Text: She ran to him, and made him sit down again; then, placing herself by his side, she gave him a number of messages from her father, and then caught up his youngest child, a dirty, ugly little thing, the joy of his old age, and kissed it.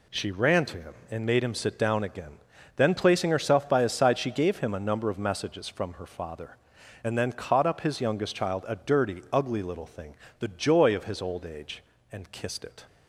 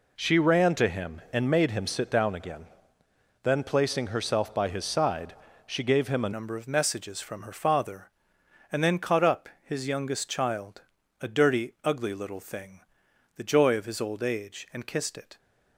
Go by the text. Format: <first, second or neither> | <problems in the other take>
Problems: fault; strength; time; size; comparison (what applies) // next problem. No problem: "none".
first | changes voice at "number"; from 6.3 s on; 9.0 s long